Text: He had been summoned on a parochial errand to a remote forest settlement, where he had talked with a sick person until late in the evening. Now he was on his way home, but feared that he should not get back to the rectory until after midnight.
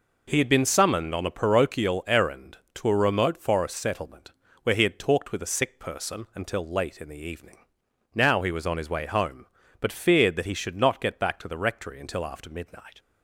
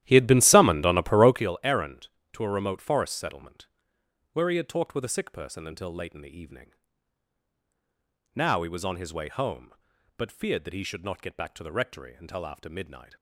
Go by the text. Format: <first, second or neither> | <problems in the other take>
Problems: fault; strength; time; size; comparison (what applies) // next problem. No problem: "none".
first | starts louder than the rest; strong; until 1.5 s; 13 dB